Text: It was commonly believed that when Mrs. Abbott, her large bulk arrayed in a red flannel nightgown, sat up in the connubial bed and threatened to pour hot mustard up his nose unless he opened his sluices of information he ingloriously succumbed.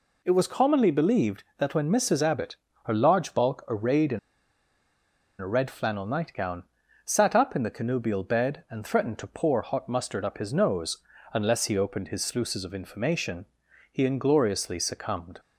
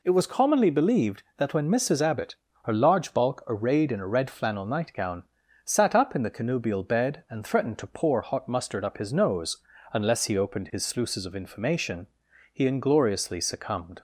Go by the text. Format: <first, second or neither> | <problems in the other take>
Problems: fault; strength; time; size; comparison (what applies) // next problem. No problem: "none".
second | pauses between "in" and "a"; at 4.1 s; 1.2 s long // pauses between "nose" and "unless"; slight; at 10.9 s; 0.34 s long; slight in the second // pauses between "information" and "he"; at 13.4 s; 0.44 s long; also in the second